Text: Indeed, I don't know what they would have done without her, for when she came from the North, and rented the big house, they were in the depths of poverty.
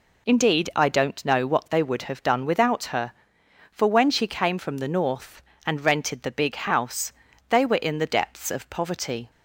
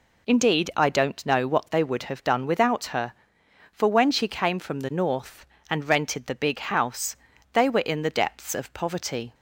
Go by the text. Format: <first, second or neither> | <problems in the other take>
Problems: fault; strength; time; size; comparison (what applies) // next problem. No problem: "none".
neither | none